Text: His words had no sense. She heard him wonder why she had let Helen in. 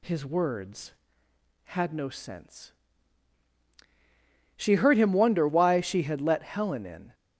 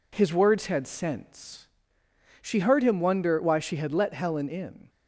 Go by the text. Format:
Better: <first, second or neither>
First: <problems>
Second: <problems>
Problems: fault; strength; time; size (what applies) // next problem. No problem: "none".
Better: first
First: none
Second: skips "no"; at 0.8 s